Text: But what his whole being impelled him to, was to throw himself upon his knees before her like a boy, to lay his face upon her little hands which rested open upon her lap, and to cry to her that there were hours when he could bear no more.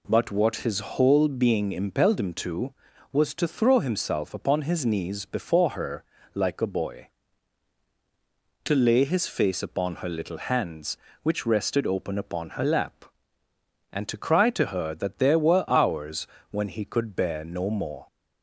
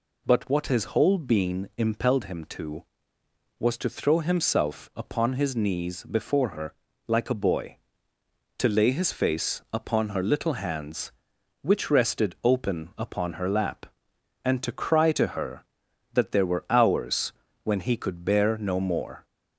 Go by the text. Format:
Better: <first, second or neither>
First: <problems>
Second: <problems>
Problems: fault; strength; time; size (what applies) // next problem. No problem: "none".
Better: neither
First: pauses between "her" and "like"; slight; at 6.0 s; 0.30 s long // pauses between "hours" and "when"; slight; at 16.2 s; 0.24 s long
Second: pauses between "her" and "like"; slight; at 6.7 s; 0.32 s long // pauses between "hours" and "when"; slight; at 17.3 s; 0.30 s long